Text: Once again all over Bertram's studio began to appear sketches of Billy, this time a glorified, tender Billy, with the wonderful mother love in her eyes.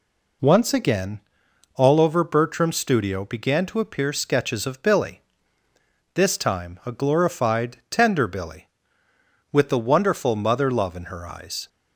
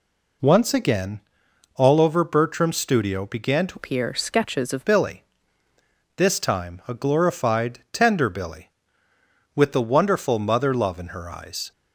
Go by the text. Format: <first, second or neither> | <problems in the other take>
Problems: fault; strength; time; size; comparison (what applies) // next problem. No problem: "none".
first | pauses between "again" and "all"; noticeable; at 1.1 s; 0.56 s long; noticeable in the first // changes voice from "appear" to "of"; from 3.7 to 4.8 s; 1.1 s long